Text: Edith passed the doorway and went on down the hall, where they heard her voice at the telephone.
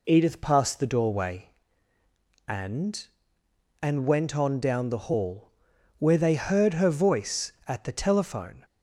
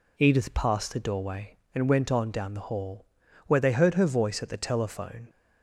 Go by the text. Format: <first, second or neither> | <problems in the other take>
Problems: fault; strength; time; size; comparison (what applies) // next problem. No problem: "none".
second | says "and" twice; at 3.8 s